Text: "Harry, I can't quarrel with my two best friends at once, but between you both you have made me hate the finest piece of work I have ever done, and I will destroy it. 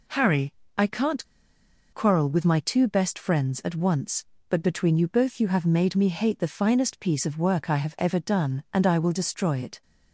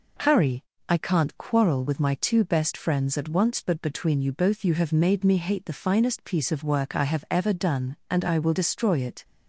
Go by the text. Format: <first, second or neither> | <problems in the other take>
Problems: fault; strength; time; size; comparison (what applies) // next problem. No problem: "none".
second | pauses between "can't" and "quarrel"; noticeable; at 1.2 s; 0.68 s long